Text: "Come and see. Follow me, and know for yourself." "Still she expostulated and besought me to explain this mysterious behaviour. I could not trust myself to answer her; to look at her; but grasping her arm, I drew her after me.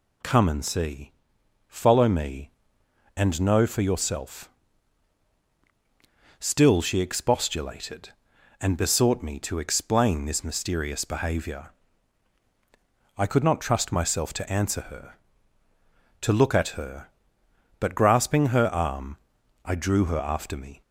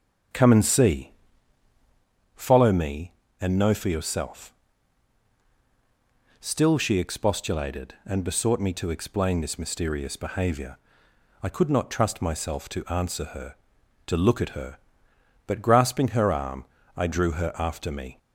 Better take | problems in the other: first | starts louder than the rest; strong; until 2.1 s; 7.5 dB

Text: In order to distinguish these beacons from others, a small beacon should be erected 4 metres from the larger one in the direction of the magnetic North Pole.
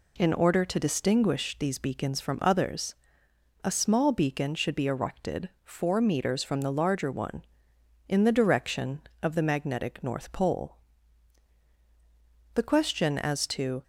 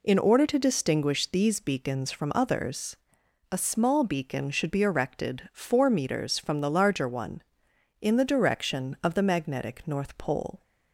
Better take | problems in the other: second | goes on to say "The question as to"; noticeable; from 12.5 s on; 1.3 s long

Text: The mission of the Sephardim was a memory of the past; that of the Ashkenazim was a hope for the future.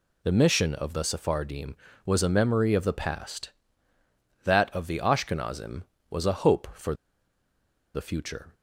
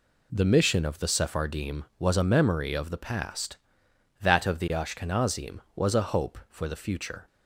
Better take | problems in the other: second | pauses between "for" and "the"; at 6.9 s; 1.0 s long

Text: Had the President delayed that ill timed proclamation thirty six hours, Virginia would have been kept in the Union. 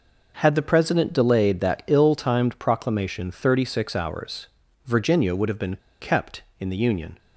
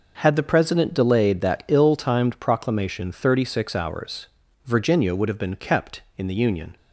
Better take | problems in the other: second | pauses between "been" and "kept"; slight; at 5.7 s; 0.22 s long

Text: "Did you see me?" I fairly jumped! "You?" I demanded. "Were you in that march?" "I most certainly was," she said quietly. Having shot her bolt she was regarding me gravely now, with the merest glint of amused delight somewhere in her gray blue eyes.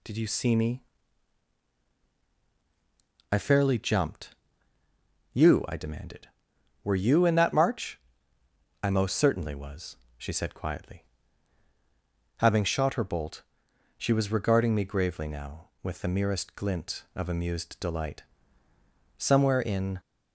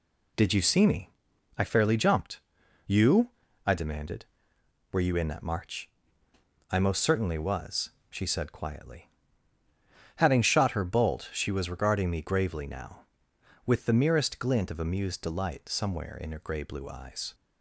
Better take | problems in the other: second | pauses between "bolt" and "she"; noticeable; at 13.4 s; 0.56 s long // pauses between "delight" and "somewhere"; noticeable; at 18.2 s; 0.94 s long // stops before "her gray blue eyes"; at 19.9 s

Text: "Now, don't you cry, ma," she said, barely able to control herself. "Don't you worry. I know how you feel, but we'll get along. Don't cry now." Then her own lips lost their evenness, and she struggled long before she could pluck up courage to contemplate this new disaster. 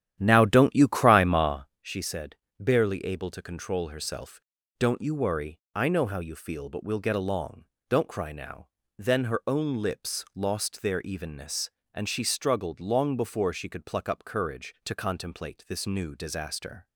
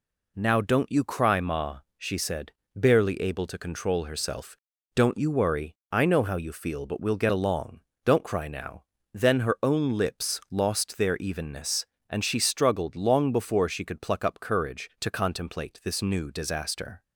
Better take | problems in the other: second | starts louder than the rest; strong; until 1.8 s; 11 dB

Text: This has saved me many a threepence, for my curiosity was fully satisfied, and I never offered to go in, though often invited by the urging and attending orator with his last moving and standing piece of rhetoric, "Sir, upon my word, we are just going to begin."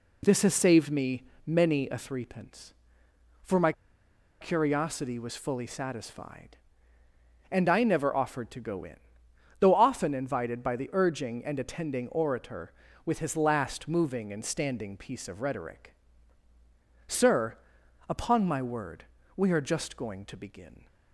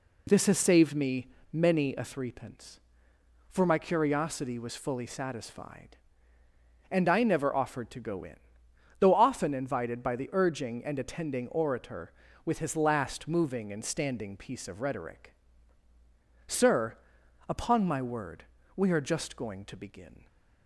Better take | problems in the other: second | pauses between "me" and "many"; slight; at 1.2 s; 0.22 s long; slight in the second // pauses between "my" and "curiosity"; noticeable; at 3.7 s; 0.68 s long

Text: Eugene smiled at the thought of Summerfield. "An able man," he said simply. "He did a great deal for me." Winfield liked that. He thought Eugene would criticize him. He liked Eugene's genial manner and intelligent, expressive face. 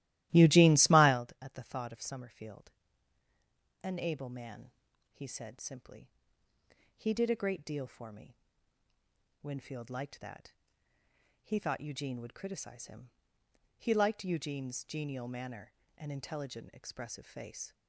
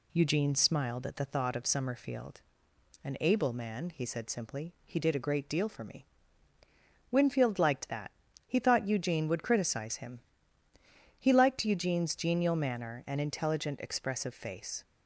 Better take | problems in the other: second | starts louder than the rest; strong; until 1.2 s; 16 dB

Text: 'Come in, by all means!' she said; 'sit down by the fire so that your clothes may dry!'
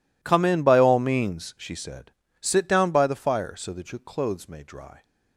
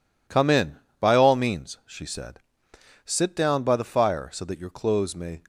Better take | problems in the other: first | stops before "dry"; at 5.4 s

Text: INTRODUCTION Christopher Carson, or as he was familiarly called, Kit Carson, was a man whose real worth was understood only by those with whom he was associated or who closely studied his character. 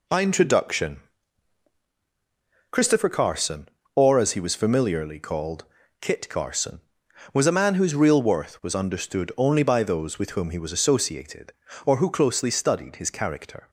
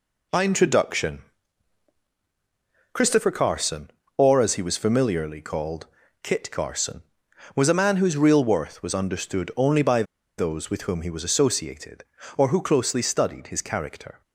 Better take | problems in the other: first | pauses between "INTRODUCTION" and "Christopher"; strong; at 1.2 s; 1.7 s long; strong in the first // pauses between "by" and "those"; slight; at 10.0 s; 0.35 s long

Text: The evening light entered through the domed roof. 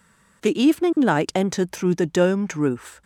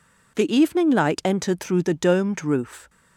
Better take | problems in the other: neither | none

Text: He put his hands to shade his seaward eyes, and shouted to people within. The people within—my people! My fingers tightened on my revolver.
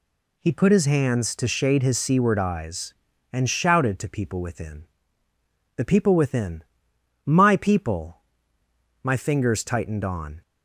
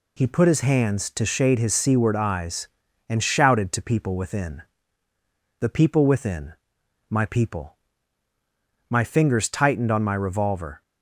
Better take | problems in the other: second | stops before "my revolver"; at 10.4 s

